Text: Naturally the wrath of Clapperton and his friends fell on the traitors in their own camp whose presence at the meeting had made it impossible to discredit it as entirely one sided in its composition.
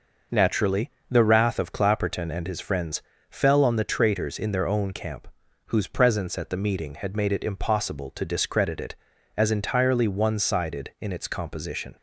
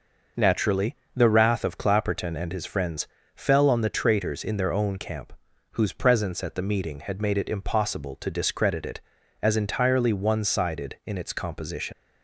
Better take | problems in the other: first | pauses between "Naturally" and "the"; slight; at 0.9 s; 0.20 s long; slight in the first // pauses between "friends" and "fell"; slight; at 3.0 s; 0.28 s long; slight in the first // pauses between "camp" and "whose"; at 5.3 s; 0.42 s long; also in the first // leaves "composition" unfinished; at 11.9 s; 80 ms

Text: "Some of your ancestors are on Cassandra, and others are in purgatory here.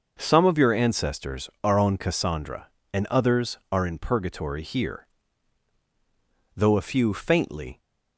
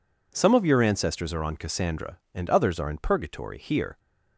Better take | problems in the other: second | goes on to say "Though a few faintly"; noticeable; from 6.5 s on; 1.2 s long

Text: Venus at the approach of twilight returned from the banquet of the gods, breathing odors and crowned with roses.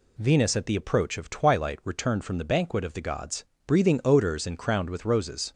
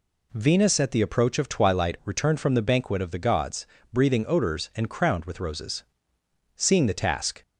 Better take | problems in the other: first | goes on to say "Seeing the task"; noticeable; from 6.5 s on; 0.86 s long

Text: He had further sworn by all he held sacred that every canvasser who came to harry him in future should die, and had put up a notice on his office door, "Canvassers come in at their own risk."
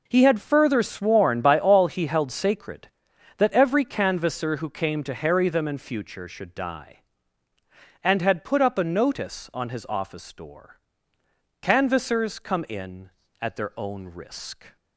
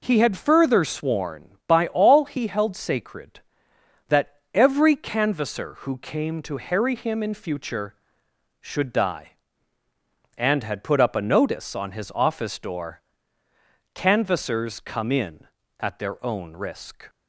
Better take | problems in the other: second | says "them" for "him"; at 5.4 s

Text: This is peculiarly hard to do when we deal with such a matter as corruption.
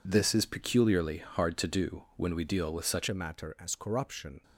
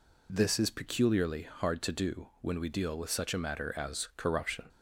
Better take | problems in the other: second | changes voice at "a"; from 3.0 s on; 1.4 s long

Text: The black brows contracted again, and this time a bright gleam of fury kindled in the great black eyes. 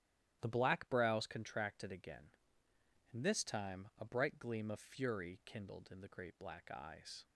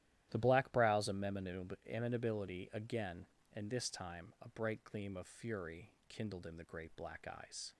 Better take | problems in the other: first | starts louder than the rest; strong; until 1.3 s; 13 dB; strong in the first // says "amenability" for "contracted"; at 1.0 s // pauses between "fury" and "kindled"; slight; at 5.8 s; 0.18 s long

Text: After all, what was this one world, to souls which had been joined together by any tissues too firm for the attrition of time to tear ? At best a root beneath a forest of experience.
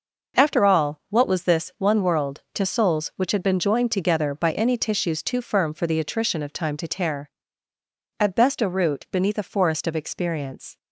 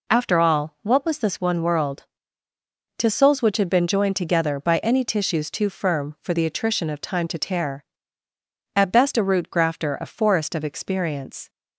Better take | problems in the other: first | says "grafter" for "beneath"; at 9.4 s

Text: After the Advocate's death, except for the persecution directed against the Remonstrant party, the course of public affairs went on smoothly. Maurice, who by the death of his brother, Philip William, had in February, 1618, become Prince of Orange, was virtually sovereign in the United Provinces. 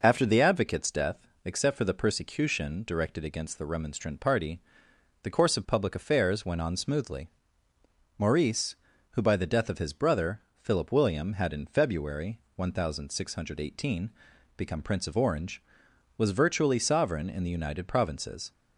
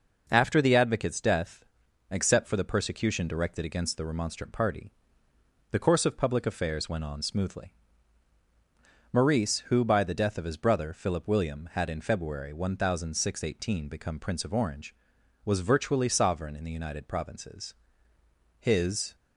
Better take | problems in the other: first | goes on to say "His"; from 18.5 s on; 0.56 s long

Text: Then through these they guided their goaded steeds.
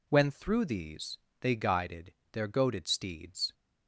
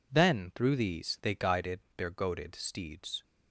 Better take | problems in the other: second | says "When" for "Then"; at 0.0 s // pauses between "these" and "they"; slight; at 1.1 s; 0.22 s long // pauses between "guided" and "their"; slight; at 2.1 s; 0.20 s long; slight in the second

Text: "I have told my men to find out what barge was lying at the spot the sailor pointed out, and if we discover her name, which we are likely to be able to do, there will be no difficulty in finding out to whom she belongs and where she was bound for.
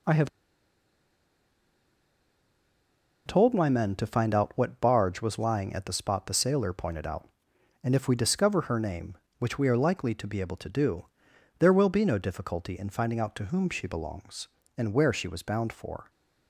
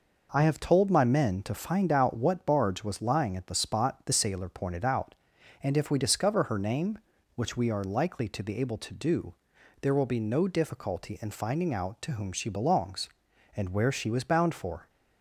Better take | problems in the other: second | pauses between "have" and "told"; strong; at 0.2 s; 2.9 s long

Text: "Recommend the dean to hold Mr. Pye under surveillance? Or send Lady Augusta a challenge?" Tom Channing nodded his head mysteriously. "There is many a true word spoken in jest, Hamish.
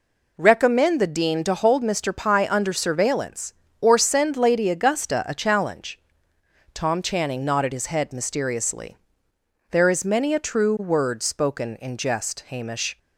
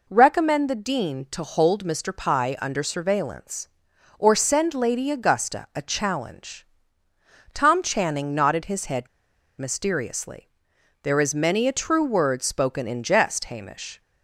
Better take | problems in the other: first | pauses between "head" and "mysteriously"; noticeable; at 9.0 s; 0.52 s long

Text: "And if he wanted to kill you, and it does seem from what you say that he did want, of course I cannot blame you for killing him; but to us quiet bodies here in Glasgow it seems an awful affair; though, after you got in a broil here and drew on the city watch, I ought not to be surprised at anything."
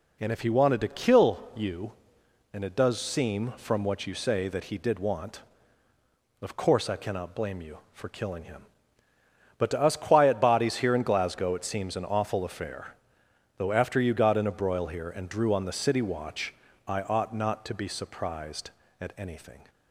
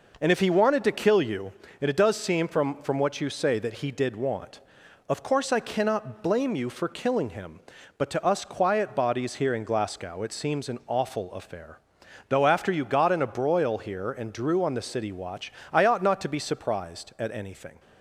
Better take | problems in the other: first | says "from" twice; at 2.8 s

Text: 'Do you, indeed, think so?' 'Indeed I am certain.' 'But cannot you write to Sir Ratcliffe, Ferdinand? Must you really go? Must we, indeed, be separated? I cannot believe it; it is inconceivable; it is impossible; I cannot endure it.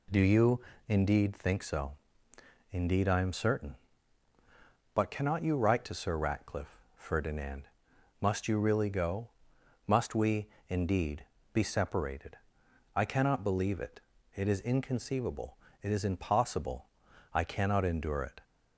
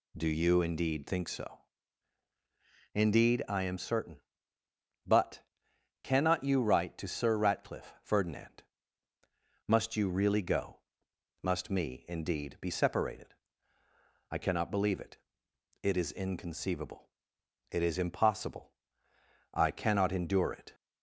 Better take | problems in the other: first | pauses between "But" and "cannot"; noticeable; at 5.4 s; 0.60 s long // says "me" for "we"; at 11.7 s

